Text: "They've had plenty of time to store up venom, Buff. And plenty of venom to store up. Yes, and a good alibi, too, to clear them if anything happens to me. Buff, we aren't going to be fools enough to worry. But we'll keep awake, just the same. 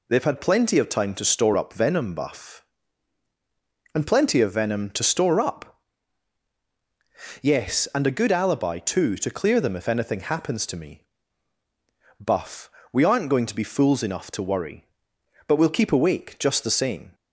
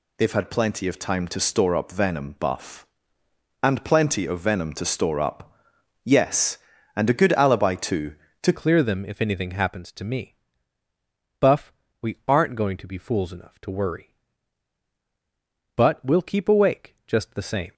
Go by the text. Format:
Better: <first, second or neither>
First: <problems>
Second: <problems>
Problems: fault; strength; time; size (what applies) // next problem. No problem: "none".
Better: first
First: none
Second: changes voice at "clear"; from 8.5 s on; 9.2 s long